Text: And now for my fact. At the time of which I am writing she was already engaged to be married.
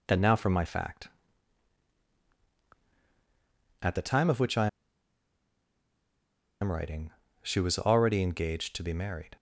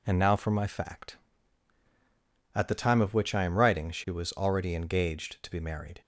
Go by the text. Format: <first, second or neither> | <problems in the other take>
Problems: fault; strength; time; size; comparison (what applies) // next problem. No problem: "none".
second | pauses between "I" and "am"; strong; at 4.6 s; 1.9 s long // pauses between "writing" and "she"; slight; at 7.1 s; 0.30 s long